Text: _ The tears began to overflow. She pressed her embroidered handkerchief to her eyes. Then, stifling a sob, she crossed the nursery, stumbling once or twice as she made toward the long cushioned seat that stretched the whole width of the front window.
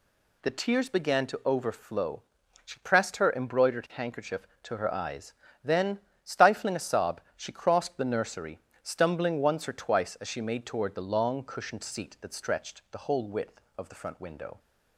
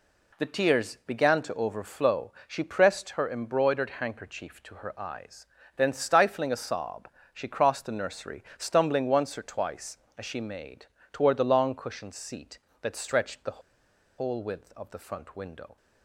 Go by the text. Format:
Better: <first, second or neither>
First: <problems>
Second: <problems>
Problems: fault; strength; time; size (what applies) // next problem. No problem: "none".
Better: first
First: none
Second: pauses between "made" and "toward"; slight; at 10.8 s; 0.26 s long // pauses between "the" and "whole"; noticeable; at 13.5 s; 0.58 s long